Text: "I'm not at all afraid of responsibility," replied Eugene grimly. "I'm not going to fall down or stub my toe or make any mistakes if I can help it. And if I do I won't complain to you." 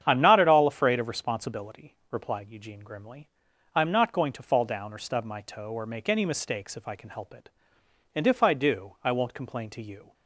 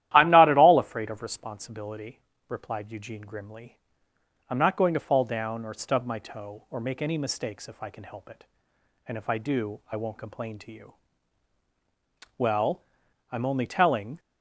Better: first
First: starts louder than the rest; strong; until 1.0 s; 8.5 dB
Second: starts louder than the rest; strong; until 1.1 s; 13 dB // goes on to say "Well I'm only telling"; strong; from 12.3 s on; 1.8 s long

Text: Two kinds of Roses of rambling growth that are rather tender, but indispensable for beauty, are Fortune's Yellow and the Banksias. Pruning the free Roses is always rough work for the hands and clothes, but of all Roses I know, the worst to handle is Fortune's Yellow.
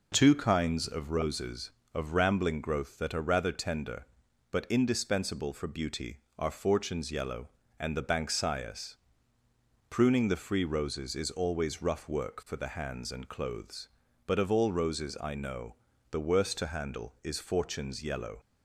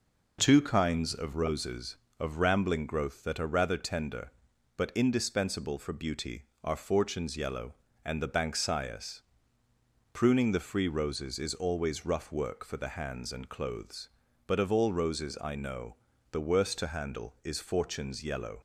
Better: neither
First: none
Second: none

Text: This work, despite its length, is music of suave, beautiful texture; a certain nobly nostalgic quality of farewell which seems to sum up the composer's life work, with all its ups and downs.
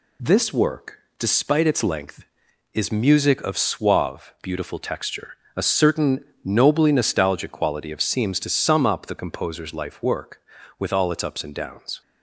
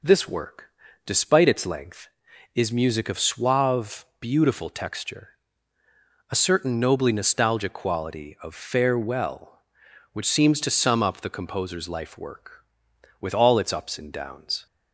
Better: second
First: pauses between "certain" and "nobly"; slight; at 6.1 s; 0.26 s long // skips "farewell which"; at 8.0 s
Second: none

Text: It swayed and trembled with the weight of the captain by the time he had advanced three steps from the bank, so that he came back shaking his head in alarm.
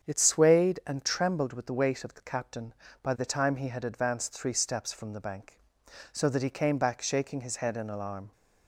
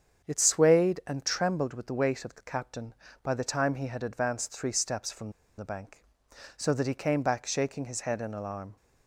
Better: first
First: starts louder than the rest; strong; until 1.0 s; 7.5 dB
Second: starts louder than the rest; strong; until 1.2 s; 7.5 dB // pauses between "from" and "the"; slight; at 5.3 s; 0.25 s long

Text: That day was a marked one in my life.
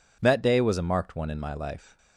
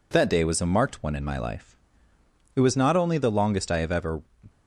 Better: first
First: none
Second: goes on to say "It was not only the longest I have ever"; strong; from 2.5 s on; 1.6 s long

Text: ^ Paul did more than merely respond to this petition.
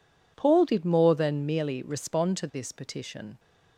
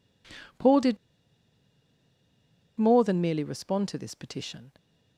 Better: first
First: none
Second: pauses between "did" and "more"; strong; at 0.9 s; 1.8 s long

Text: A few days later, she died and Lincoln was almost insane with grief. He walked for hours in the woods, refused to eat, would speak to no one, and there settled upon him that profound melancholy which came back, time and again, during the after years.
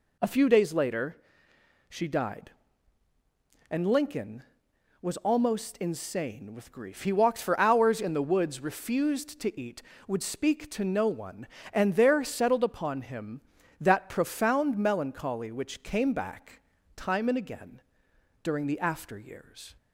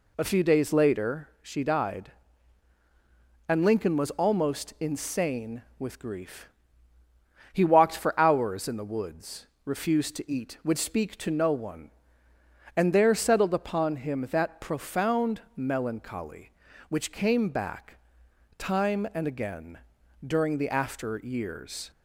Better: neither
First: none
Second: none

